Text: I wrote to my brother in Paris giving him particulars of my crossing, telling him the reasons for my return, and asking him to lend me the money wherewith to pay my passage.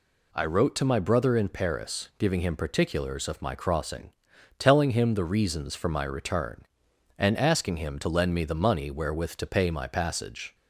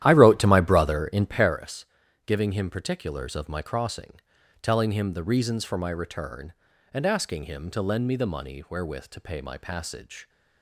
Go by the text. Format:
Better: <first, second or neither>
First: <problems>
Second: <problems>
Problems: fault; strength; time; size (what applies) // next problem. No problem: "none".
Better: first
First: none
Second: starts louder than the rest; strong; until 1.6 s; 12 dB // pauses between "Paris" and "giving"; at 1.8 s; 0.40 s long